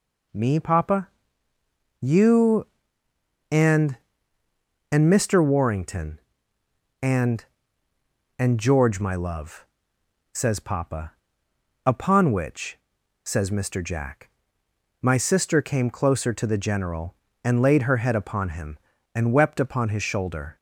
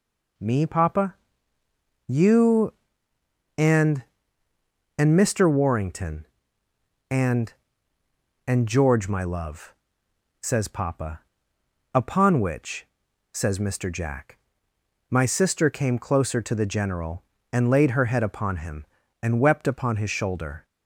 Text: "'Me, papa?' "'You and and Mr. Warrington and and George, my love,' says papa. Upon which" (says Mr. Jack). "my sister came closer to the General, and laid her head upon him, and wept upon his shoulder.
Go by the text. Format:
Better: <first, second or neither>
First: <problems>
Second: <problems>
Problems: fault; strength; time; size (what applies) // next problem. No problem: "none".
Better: neither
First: none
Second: none